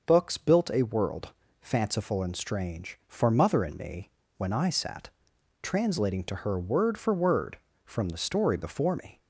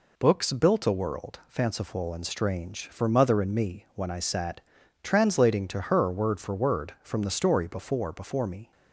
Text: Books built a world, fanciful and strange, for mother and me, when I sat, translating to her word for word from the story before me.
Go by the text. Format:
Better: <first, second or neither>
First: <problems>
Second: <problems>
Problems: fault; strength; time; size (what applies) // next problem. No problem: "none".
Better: first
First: none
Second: says "before" twice; at 8.1 s